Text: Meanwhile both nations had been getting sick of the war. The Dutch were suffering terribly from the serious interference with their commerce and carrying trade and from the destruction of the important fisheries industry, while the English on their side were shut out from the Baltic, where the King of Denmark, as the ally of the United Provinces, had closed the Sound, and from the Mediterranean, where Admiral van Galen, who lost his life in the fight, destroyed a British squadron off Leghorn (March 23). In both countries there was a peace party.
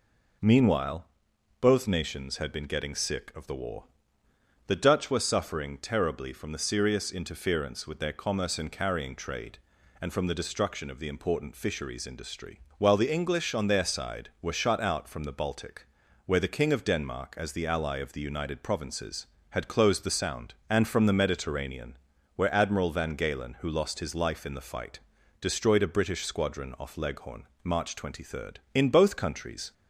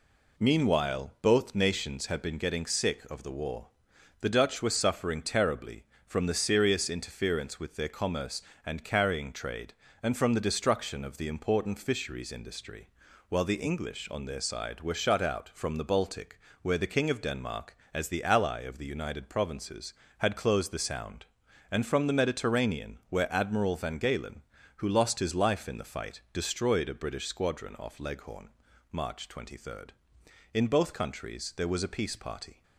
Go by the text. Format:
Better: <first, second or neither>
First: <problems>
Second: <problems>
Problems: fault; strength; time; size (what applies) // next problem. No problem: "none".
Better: second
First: pauses between "Meanwhile" and "both"; noticeable; at 1.0 s; 0.56 s long // stops before "there was a peace party"; at 29.7 s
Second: none